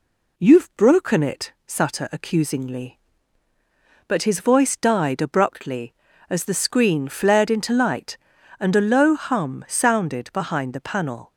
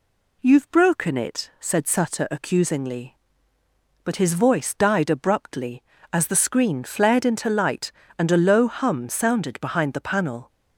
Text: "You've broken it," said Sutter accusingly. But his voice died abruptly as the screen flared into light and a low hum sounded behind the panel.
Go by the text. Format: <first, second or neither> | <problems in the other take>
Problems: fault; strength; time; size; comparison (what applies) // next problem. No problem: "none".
second | skips "said"; at 1.5 s